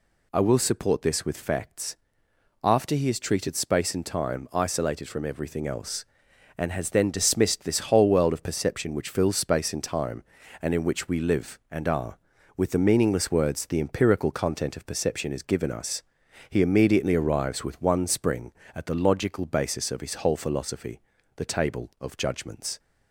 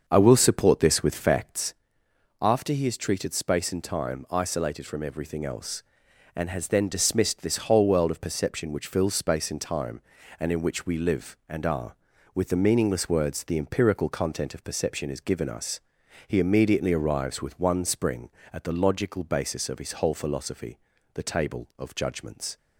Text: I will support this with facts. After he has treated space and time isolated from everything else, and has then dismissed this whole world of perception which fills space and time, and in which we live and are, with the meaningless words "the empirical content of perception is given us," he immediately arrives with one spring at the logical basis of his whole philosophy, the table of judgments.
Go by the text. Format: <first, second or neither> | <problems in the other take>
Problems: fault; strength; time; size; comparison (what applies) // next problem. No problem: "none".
first | starts louder than the rest; until 1.8 s; 6.5 dB